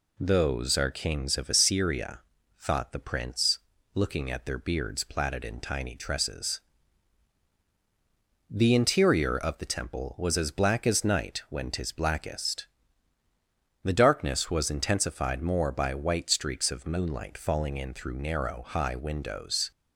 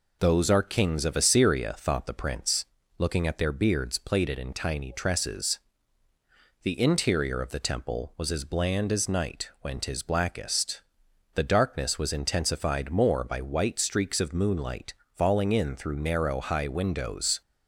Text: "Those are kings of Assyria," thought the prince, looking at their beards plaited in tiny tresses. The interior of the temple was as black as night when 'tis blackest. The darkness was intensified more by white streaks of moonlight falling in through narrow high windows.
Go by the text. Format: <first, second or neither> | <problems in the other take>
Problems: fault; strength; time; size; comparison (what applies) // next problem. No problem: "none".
first | says "bland" for "black"; at 8.4 s // pauses between "moonlight" and "falling"; slight; at 14.9 s; 0.22 s long